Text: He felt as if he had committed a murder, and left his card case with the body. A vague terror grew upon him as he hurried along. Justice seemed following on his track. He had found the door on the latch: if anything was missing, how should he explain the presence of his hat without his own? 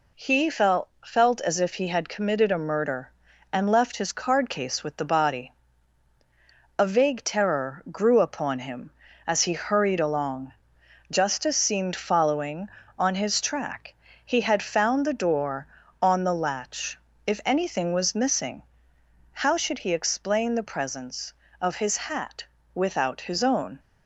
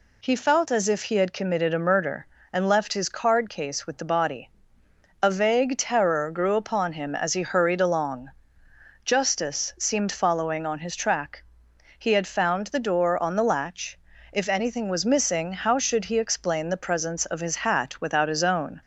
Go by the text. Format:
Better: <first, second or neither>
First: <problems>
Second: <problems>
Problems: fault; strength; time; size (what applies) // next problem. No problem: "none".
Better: second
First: says "felt" twice; at 1.0 s // pauses between "hat" and "without"; slight; at 22.4 s; 0.32 s long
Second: none